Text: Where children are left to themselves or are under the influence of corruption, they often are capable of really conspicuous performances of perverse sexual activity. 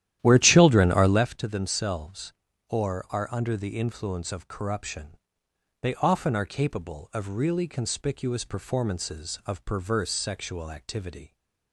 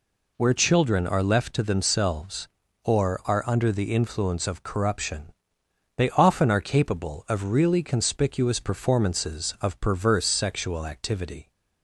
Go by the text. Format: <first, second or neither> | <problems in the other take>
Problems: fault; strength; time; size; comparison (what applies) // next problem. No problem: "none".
second | starts louder than the rest; strong; until 1.3 s; 12 dB